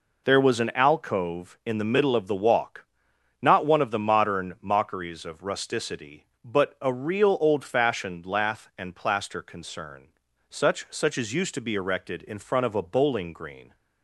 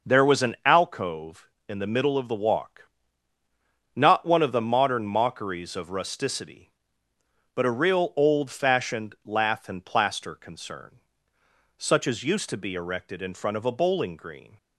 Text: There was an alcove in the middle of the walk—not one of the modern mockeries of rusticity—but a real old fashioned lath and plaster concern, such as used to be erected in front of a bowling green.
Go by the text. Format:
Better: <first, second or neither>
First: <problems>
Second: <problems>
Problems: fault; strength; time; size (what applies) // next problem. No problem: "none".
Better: second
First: says "such" twice; at 10.8 s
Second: none